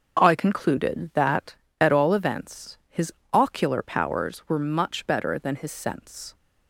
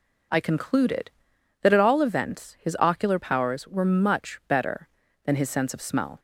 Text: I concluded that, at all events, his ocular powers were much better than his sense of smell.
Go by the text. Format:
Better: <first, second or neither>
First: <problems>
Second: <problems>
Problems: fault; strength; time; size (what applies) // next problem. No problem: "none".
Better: second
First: starts louder than the rest; until 1.2 s; 6.5 dB // pauses between "his" and "ocular"; slight; at 3.1 s; 0.20 s long // stops before "of smell"; at 6.3 s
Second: none